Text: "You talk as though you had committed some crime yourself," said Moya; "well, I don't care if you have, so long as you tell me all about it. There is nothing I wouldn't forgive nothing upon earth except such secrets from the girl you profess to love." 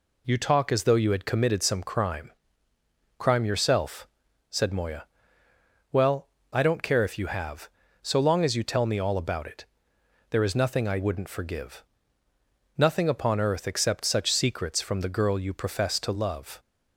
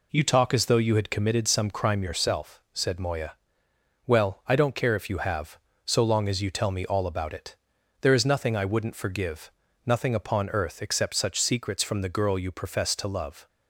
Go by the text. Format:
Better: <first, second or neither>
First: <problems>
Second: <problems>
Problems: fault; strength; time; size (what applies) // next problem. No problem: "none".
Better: second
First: says "crime" twice; at 3.1 s // pauses between "forgive" and "nothing"; noticeable; at 11.8 s; 0.92 s long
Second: pauses between "forgive" and "nothing"; slight; at 9.5 s; 0.34 s long